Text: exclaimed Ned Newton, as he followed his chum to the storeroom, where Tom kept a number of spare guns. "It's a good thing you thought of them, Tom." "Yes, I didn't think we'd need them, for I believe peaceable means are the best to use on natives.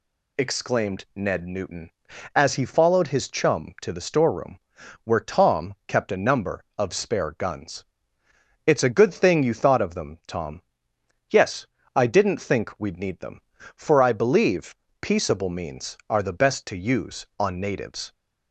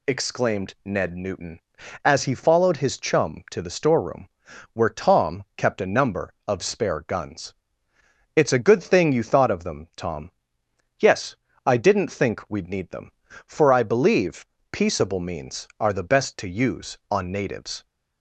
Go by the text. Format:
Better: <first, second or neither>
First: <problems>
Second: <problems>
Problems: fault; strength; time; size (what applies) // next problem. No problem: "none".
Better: neither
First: pauses between "believe" and "peaceable"; slight; at 14.7 s; 0.24 s long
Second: pauses between "believe" and "peaceable"; slight; at 14.4 s; 0.24 s long